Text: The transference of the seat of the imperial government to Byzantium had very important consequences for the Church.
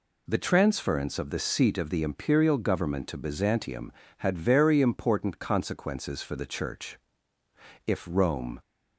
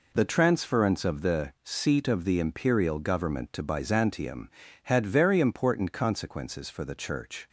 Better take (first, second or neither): second